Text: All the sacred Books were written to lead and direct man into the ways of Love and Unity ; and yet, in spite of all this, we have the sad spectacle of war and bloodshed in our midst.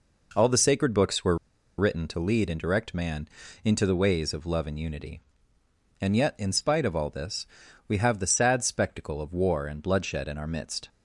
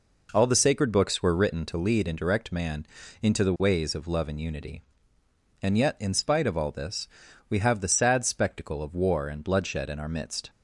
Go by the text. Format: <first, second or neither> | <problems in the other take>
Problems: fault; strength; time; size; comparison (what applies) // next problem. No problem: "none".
second | pauses between "were" and "written"; at 1.3 s; 0.42 s long // pauses between "man" and "into"; slight; at 3.2 s; 0.34 s long; slight in the second